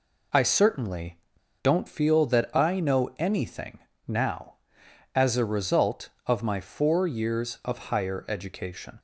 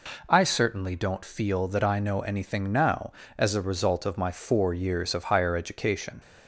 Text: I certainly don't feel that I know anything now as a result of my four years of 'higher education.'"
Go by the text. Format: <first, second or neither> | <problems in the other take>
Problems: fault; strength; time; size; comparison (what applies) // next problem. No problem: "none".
second | pauses between "certainly" and "don't"; at 1.1 s; 0.41 s long // pauses between "anything" and "now"; slight; at 3.7 s; 0.28 s long